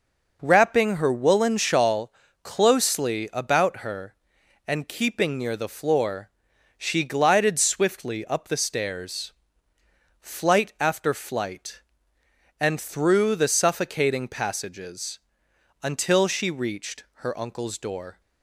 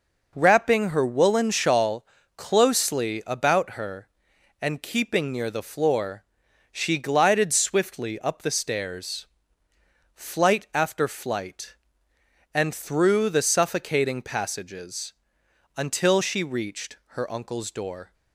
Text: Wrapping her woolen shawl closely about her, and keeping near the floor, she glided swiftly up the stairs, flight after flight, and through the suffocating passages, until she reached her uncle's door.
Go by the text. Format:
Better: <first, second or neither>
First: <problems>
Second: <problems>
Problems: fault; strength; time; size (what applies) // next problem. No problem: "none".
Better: neither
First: pauses between "shawl" and "closely"; slight; at 2.1 s; 0.32 s long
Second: pauses between "shawl" and "closely"; slight; at 2.0 s; 0.32 s long